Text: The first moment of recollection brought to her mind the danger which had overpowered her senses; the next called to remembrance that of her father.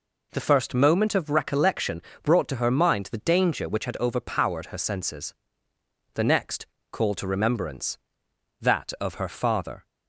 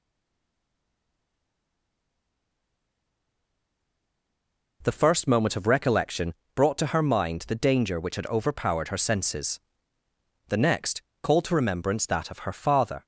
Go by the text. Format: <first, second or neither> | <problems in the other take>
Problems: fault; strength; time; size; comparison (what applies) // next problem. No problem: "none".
first | stays silent before the first word; strong; until 4.8 s; 4.8 s long // pauses between "recollection" and "brought"; slight; at 6.3 s; 0.22 s long; slight in the first // pauses between "next" and "called"; slight; at 11.0 s; 0.18 s long; slight in the first